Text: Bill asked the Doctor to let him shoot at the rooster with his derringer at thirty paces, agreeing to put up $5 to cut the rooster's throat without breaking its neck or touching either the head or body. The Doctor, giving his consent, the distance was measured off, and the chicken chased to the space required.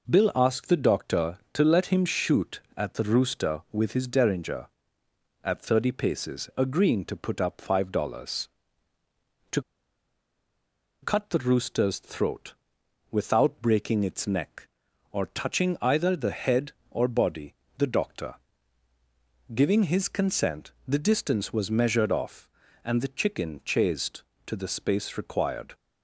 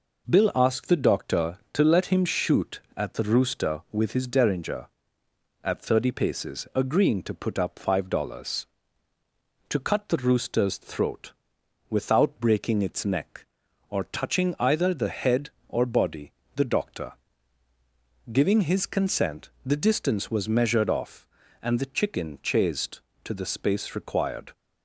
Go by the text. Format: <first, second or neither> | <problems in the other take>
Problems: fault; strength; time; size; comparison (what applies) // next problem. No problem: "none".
second | pauses between "to" and "cut"; strong; at 9.6 s; 1.4 s long // pauses between "throat" and "without"; noticeable; at 12.5 s; 0.56 s long; noticeable in the second